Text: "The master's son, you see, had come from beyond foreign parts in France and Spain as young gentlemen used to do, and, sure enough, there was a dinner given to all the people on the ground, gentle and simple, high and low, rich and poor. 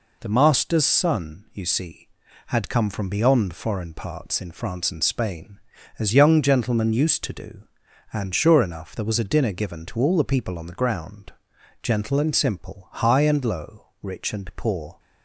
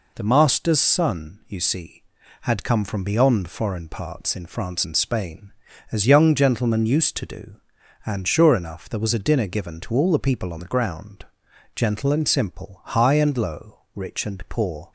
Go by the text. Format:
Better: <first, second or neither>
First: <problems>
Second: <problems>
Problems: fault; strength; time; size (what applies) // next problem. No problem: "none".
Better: neither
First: none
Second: none